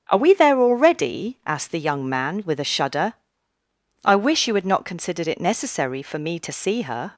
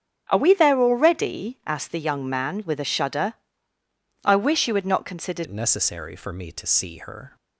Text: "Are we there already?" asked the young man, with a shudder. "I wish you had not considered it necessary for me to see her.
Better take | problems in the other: first | starts louder than the rest; strong; until 1.3 s; 9.5 dB; strong in the first // changes voice at "it"; from 5.4 s on; 1.9 s long

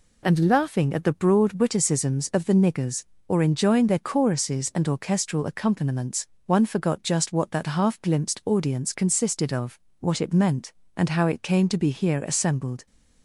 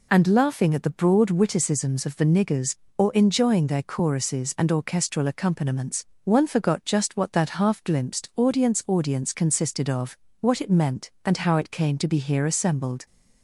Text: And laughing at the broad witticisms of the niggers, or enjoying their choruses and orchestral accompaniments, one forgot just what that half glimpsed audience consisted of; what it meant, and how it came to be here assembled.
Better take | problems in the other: first | says "audience" twice; at 8.8 s

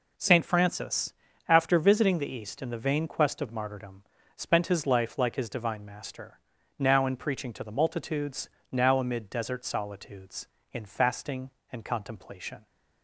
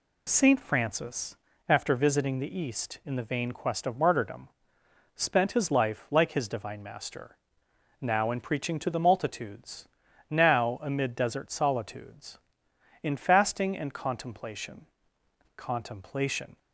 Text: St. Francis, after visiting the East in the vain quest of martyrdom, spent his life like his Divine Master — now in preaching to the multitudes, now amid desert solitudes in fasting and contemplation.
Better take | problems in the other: first | says "contemplation" twice; at 15.5 s

